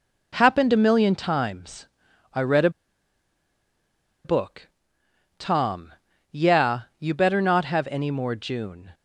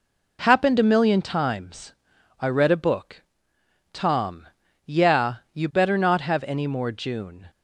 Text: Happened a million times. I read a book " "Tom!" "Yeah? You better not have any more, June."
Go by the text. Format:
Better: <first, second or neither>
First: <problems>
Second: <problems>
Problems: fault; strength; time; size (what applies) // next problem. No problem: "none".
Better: second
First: pauses between "a" and "book"; strong; at 2.6 s; 1.5 s long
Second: none